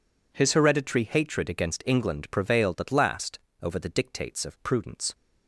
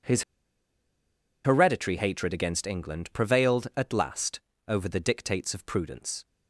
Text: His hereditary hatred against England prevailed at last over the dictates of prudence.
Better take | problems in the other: first | pauses between "His" and "hereditary"; at 0.2 s; 1.2 s long // pauses between "last" and "over"; slight; at 4.3 s; 0.28 s long; slight in the first

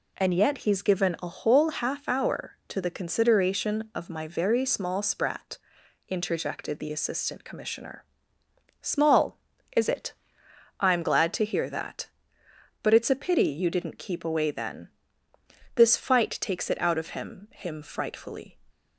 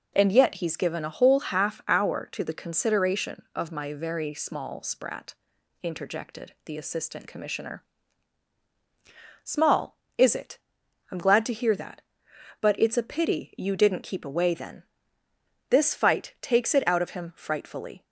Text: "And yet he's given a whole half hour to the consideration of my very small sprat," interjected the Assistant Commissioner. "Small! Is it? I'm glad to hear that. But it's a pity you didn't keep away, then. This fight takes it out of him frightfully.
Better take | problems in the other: second | says "him" twice; at 17.5 s

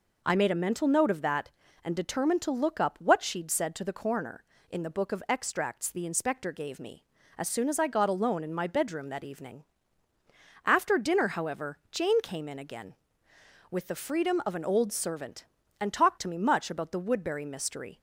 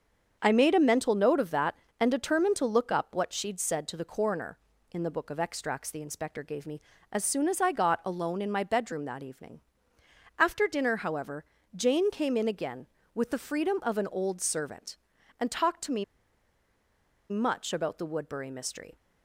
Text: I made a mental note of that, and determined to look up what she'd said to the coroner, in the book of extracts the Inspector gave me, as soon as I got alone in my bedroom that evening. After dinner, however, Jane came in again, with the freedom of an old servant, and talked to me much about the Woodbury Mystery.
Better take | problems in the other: first | starts louder than the rest; until 1.4 s; 7 dB // pauses between "me" and "much"; strong; at 16.0 s; 1.2 s long

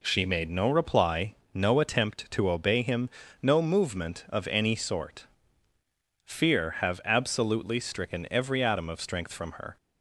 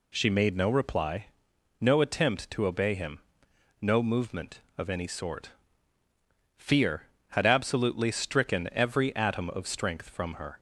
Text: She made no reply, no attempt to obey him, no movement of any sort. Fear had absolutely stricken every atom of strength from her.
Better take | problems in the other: second | says "have" for "had"; at 6.8 s

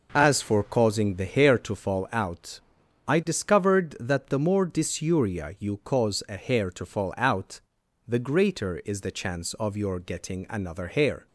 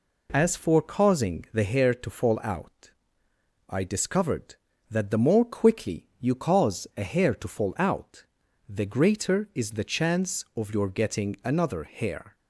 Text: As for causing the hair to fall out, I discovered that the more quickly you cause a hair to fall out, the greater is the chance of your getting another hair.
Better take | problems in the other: second | says "dysuria" for "quickly"; at 4.6 s

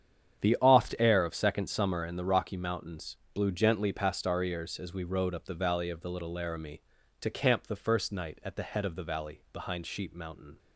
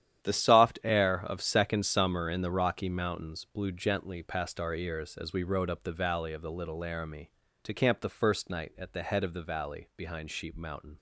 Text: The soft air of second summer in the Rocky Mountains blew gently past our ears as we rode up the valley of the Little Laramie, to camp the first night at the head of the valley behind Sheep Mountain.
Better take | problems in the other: second | starts louder than the rest; strong; until 1.5 s; 9 dB; strong in the second // says "oft" for "soft"; at 0.6 s // pauses between "Mountains" and "blew"; slight; at 3.1 s; 0.18 s long

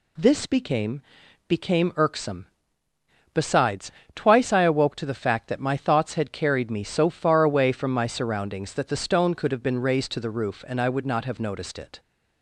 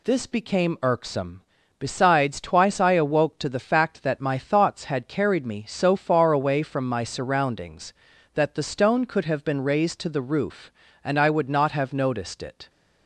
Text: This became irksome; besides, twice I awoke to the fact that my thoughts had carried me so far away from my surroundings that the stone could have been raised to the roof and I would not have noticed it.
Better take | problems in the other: second | says "became" twice; at 1.4 s

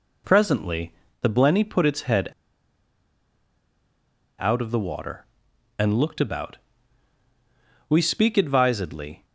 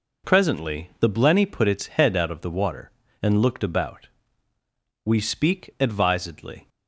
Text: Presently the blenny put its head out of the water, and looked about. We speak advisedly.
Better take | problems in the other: second | pauses between "Presently" and "the"; slight; at 0.9 s; 0.30 s long // pauses between "head" and "out"; strong; at 2.2 s; 2.0 s long

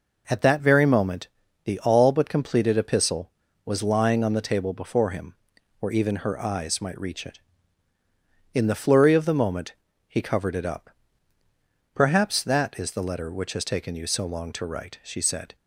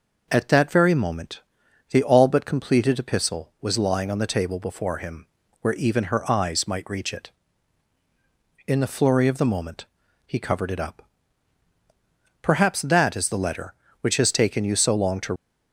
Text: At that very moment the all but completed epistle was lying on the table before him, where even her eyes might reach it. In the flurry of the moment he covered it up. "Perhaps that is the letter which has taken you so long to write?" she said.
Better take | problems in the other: first | pauses between "moment" and "the"; noticeable; at 1.4 s; 0.50 s long; slight in the first // pauses between "moment" and "he"; at 9.8 s; 0.40 s long; slight in the first // stops before "write she said"; at 15.3 s

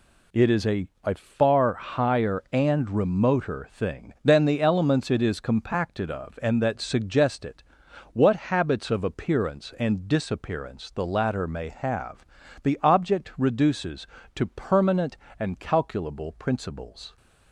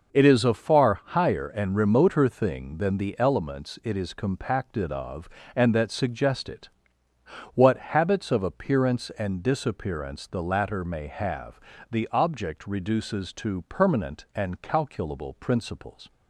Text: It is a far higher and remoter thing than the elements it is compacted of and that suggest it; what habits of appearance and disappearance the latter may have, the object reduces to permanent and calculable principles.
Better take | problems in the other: second | says "a" twice; at 1.0 s

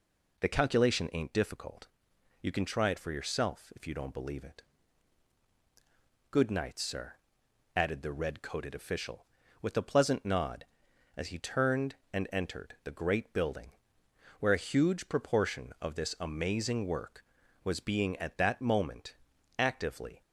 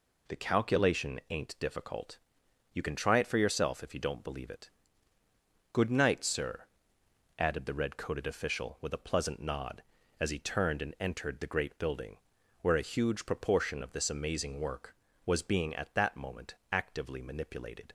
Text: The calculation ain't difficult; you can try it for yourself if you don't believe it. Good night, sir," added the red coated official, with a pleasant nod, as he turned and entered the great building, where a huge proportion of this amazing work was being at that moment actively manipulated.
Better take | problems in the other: second | pauses between "moment" and "actively"; at 19.1 s; 0.42 s long; slight in the second // stops before "manipulated"; at 20.2 s

